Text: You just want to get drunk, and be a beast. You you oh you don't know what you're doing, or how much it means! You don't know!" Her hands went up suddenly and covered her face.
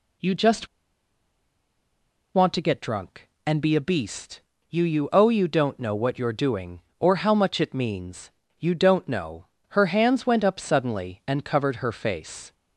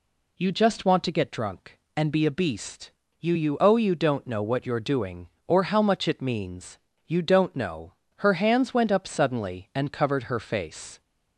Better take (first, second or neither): second